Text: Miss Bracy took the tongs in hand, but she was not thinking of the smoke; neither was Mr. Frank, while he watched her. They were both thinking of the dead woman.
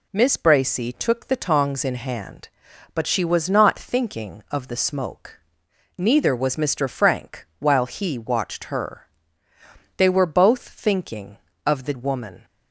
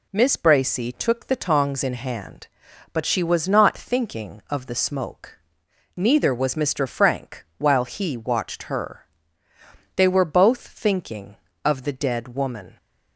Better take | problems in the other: second | skips "dead"; at 11.9 s

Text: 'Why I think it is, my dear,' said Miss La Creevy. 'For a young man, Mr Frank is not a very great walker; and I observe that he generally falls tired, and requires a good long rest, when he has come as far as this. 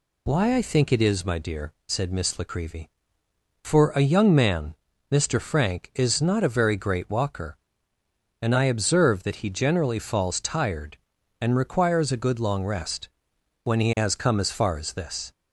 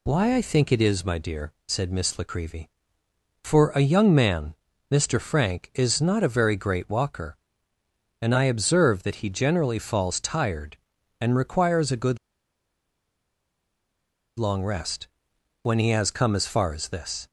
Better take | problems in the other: first | pauses between "good" and "long"; strong; at 12.1 s; 2.2 s long

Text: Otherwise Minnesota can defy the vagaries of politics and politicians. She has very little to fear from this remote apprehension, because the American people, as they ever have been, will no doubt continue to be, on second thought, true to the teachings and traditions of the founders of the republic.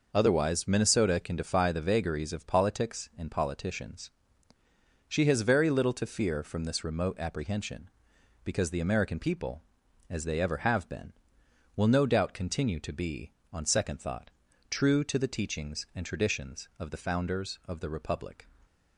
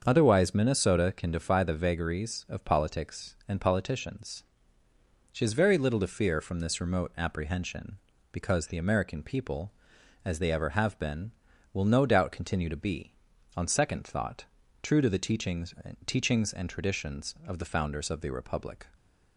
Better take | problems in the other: first | starts louder than the rest; until 1.0 s; 7 dB // says "teachings" twice; at 16.0 s

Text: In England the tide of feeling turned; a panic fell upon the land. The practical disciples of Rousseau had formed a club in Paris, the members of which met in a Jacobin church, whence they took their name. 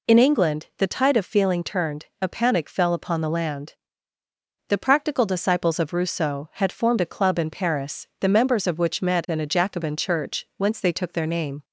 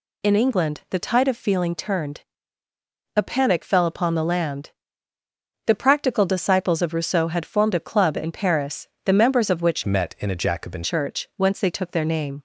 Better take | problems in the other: first | changes voice from "met" to "Jacobin"; from 9.8 to 10.8 s; 1.0 s long

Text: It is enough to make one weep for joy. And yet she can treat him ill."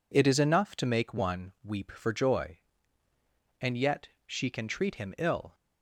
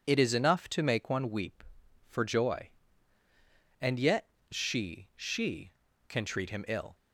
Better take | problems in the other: first | pauses between "yet" and "she"; slight; at 4.2 s; 0.24 s long; slight in the first // says "she" twice; at 5.1 s

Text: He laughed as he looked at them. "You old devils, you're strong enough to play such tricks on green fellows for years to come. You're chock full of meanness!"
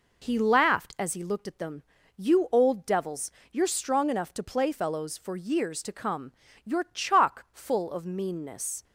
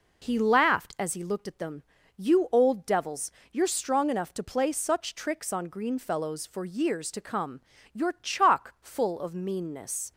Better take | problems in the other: second | skips "such tricks on green"; at 4.7 s

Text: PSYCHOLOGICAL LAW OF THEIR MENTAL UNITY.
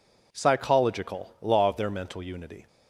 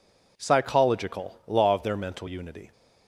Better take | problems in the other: neither | none

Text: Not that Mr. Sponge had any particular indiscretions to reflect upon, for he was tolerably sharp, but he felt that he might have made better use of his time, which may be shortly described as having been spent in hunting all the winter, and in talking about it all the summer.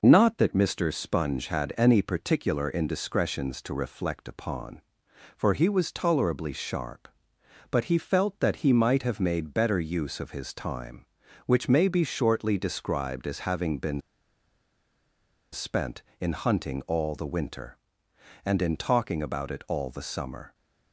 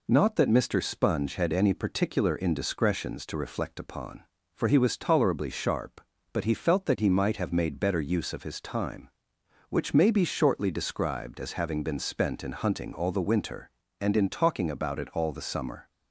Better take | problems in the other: second | pauses between "been" and "spent"; strong; at 14.0 s; 1.5 s long

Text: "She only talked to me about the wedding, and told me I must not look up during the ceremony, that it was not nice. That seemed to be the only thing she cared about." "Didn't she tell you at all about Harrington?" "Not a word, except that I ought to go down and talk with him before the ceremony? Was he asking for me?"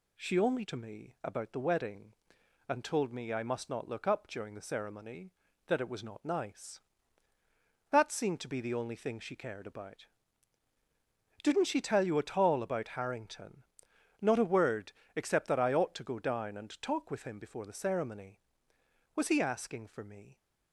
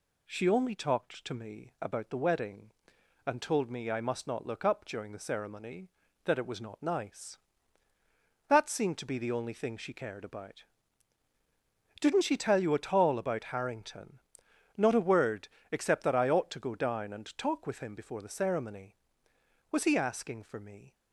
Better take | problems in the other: second | skips "talked"; at 0.6 s

